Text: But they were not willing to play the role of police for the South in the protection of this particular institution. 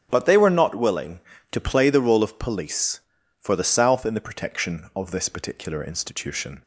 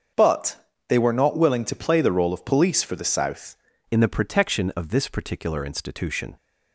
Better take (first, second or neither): first